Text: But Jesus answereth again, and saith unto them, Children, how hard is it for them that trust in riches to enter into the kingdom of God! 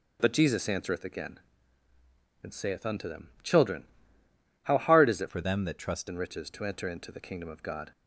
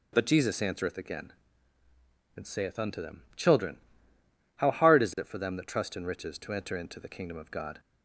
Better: second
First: starts louder than the rest; until 1.2 s; 7 dB // changes voice from "for" to "trust"; from 5.2 to 6.0 s; 0.8 s long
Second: starts louder than the rest; until 1.1 s; 7 dB

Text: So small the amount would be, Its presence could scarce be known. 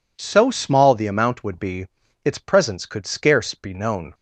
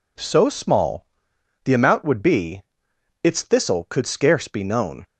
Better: first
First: none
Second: pauses between "small" and "the"; noticeable; at 1.0 s; 0.60 s long // says "thistle" for "presence"; at 3.4 s

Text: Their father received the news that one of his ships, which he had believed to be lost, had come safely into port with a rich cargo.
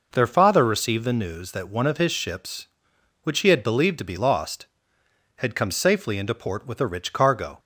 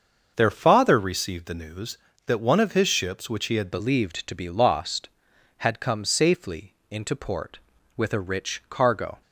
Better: first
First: none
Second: starts louder than the rest; until 1.3 s; 6.5 dB // changes voice at "believed"; from 3.7 s on; 5.5 s long // pauses between "safely" and "into"; slight; at 6.7 s; 0.16 s long

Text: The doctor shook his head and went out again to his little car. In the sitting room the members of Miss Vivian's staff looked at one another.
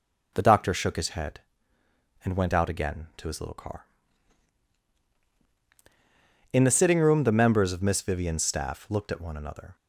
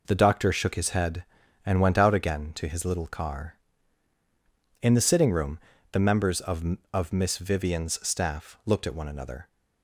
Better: first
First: none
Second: pauses between "room" and "the"; slight; at 5.5 s; 0.32 s long // says "of" twice; at 6.9 s

